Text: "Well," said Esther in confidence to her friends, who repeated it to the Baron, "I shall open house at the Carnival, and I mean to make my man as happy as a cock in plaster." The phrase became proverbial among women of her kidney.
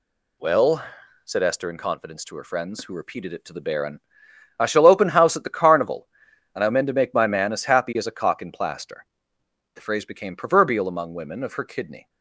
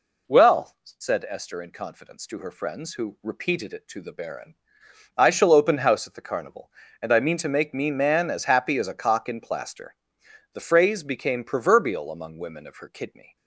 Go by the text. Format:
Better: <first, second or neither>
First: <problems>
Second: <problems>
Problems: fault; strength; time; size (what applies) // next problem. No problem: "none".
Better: first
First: none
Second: says "me" for "my"; at 7.7 s